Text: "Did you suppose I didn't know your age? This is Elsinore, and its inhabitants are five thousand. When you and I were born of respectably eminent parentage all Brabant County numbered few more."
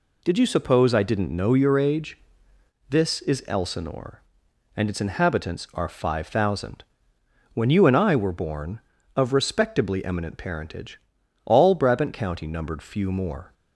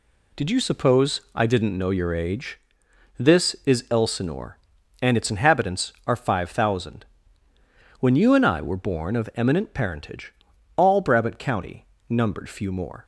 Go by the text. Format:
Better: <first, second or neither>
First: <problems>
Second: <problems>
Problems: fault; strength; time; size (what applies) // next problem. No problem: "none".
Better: first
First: pauses between "parentage" and "all"; noticeable; at 10.9 s; 0.46 s long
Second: skips "respectably"; at 9.3 s // pauses between "parentage" and "all"; at 10.3 s; 0.42 s long // pauses between "County" and "numbered"; slight; at 11.8 s; 0.24 s long